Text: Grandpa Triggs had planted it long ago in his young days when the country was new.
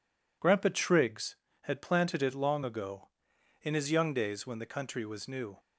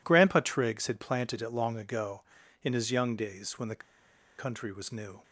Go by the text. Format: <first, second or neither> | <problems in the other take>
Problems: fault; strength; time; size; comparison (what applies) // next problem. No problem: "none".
first | pauses between "the" and "country"; noticeable; at 3.8 s; 0.58 s long